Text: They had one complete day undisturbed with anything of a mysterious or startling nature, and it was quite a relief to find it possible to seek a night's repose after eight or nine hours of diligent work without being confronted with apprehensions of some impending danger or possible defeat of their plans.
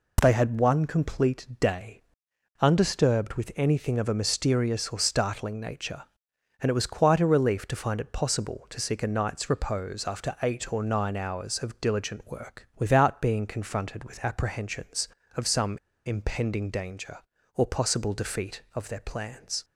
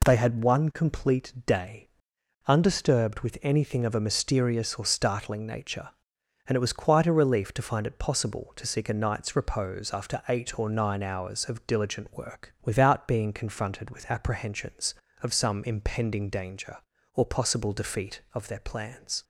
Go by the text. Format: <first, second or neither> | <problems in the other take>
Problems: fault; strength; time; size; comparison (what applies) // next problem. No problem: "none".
second | pauses between "day" and "undisturbed"; noticeable; at 2.0 s; 0.56 s long; noticeable in the second // pauses between "some" and "impending"; slight; at 15.7 s; 0.28 s long